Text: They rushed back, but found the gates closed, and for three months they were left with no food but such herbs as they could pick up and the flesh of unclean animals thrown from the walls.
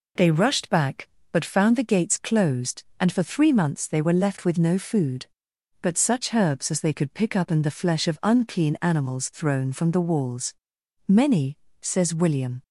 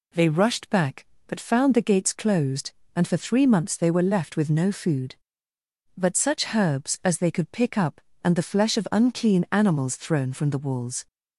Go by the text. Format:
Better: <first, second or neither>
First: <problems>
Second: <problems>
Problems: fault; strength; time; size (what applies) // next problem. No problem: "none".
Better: second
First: goes on to say "Many says William"; from 11.0 s on; 1.5 s long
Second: none